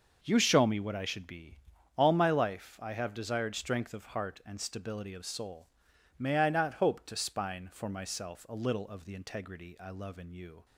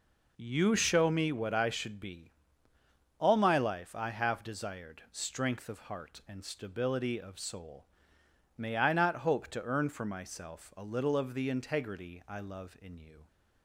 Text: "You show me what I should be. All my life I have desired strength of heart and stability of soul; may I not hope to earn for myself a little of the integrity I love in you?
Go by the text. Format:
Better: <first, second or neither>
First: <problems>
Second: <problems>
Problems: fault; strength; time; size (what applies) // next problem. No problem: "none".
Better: second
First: starts louder than the rest; noticeable; until 1.2 s; 6 dB // says "spine" for "earn"; at 7.1 s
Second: none